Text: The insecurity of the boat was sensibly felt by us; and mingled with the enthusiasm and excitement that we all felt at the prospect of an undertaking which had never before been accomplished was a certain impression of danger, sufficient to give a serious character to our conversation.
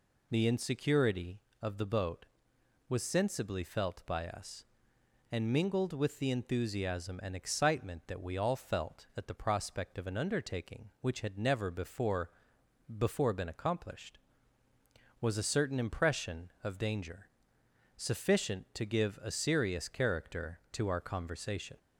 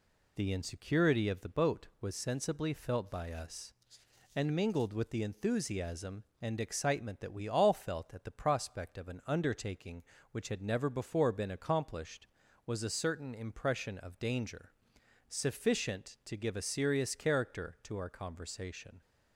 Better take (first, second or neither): second